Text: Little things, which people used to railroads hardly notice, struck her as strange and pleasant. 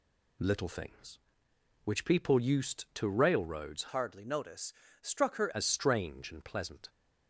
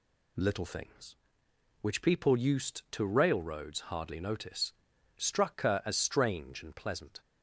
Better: second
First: changes voice from "hardly" to "her"; from 3.8 to 5.4 s; 1.6 s long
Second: none

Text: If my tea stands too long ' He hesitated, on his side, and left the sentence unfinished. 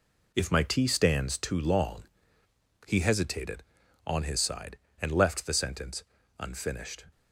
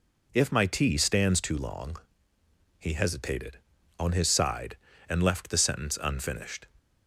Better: second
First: gets quieter; throughout; 3.5 dB // pauses between "sentence" and "unfinished"; slight; at 6.0 s; 0.36 s long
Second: none

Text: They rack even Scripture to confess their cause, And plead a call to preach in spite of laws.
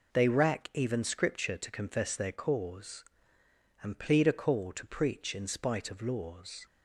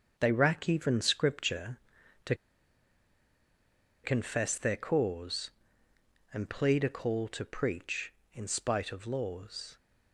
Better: first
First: none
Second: starts louder than the rest; until 1.1 s; 6.5 dB // pauses between "to" and "confess"; strong; at 2.3 s; 1.6 s long

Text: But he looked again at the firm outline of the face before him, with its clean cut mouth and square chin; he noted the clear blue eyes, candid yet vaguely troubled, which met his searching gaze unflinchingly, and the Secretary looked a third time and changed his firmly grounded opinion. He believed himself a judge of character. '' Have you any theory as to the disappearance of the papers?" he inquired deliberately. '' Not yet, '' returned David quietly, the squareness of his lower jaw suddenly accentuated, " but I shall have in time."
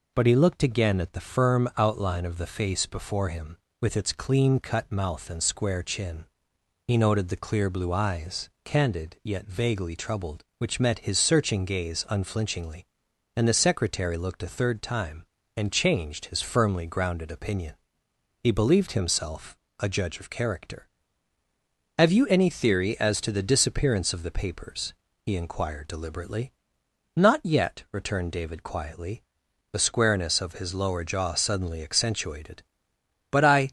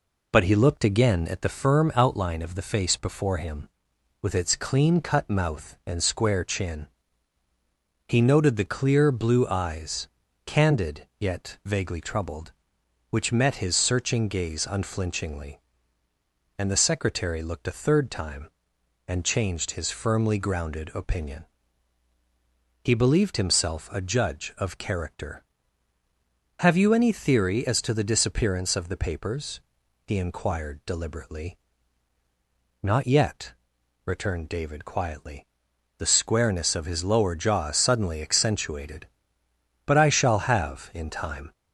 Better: second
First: pauses between "himself" and "a"; slight; at 19.5 s; 0.22 s long // stops before "shall have in time"; at 33.6 s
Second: none

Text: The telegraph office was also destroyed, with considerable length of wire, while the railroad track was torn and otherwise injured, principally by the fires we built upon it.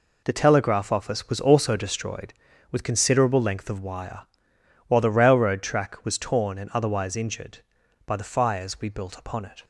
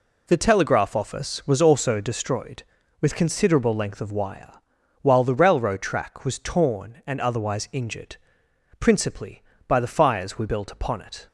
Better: second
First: skips "principally"; at 7.8 s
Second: none

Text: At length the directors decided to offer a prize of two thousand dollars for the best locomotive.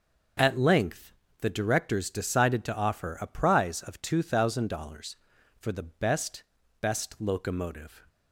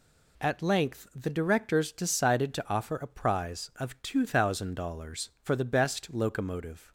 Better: second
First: starts louder than the rest; noticeable; until 1.6 s; 6 dB // pauses between "length" and "the"; slight; at 1.1 s; 0.30 s long // says "best" twice; at 6.8 s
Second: none

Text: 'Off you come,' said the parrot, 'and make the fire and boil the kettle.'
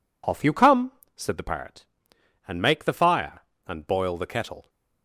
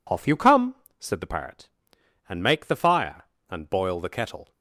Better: neither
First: none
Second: none

